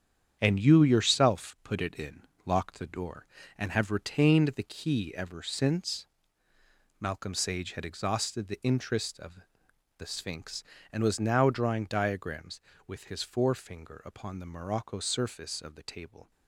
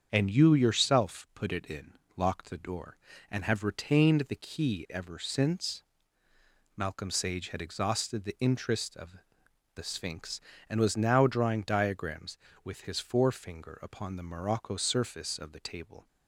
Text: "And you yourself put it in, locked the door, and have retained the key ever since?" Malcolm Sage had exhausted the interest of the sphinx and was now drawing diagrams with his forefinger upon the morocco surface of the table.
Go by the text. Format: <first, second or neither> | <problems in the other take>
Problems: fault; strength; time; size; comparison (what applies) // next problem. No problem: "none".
second | gets quieter; strong; throughout; 8.5 dB // starts louder than the rest; strong; until 1.4 s; 8.5 dB; strong in the second // pauses between "of" and "the"; noticeable; at 9.4 s; 0.58 s long; noticeable in the second